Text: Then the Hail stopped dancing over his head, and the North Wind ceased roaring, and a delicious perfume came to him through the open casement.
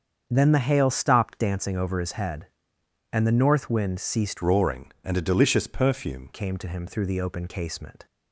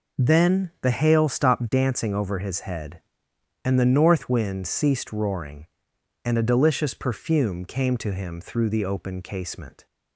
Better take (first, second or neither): second